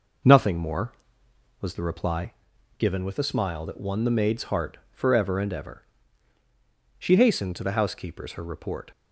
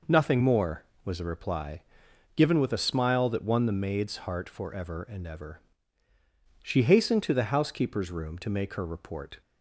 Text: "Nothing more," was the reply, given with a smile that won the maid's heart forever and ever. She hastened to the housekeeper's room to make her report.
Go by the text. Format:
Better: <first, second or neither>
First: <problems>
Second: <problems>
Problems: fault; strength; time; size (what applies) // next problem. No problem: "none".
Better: second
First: skips "room to make"; at 8.3 s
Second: none